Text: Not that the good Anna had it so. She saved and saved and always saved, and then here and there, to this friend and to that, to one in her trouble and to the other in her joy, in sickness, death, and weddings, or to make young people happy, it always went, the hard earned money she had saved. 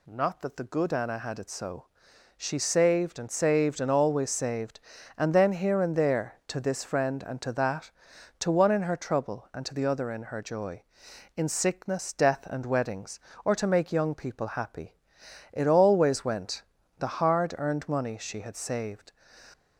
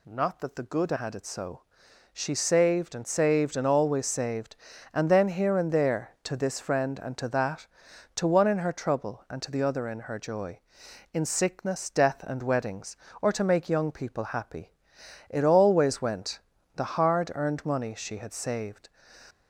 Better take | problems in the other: first | skips "Anna"; at 0.9 s

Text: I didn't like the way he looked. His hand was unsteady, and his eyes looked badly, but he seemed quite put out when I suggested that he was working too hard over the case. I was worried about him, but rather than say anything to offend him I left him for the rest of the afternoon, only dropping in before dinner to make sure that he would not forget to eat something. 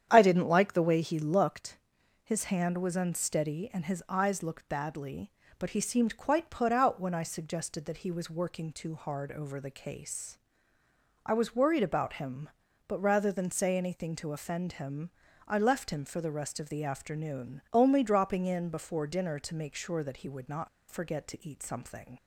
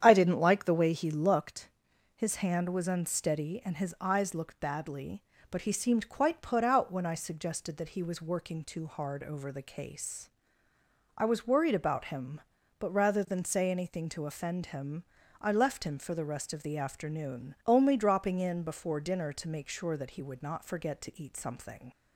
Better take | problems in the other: second | starts louder than the rest; strong; until 1.1 s; 9 dB; strong in the second // pauses between "him" and "I"; at 15.1 s; 0.40 s long; also in the second // pauses between "not" and "forget"; slight; at 20.6 s; 0.21 s long

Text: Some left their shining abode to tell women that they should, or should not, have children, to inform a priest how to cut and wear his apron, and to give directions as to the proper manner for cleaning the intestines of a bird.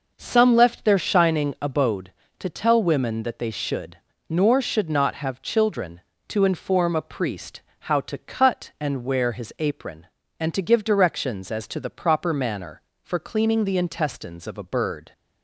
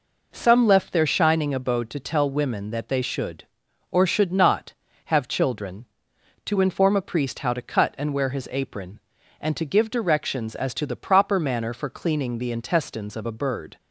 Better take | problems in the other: second | says "nor" for "or"; at 4.2 s // pauses between "priest" and "how"; slight; at 7.6 s; 0.18 s long

